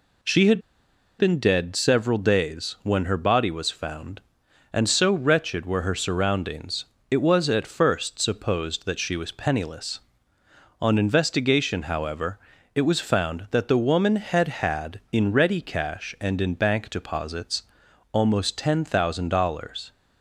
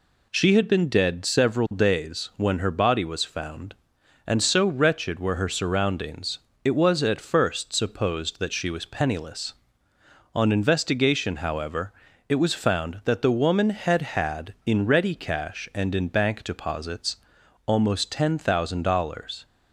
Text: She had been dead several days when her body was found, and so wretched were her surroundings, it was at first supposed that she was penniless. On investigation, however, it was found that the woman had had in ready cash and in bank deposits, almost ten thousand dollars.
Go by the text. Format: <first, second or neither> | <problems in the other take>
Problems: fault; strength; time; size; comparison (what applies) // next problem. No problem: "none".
second | pauses between "had" and "been"; noticeable; at 0.6 s; 0.57 s long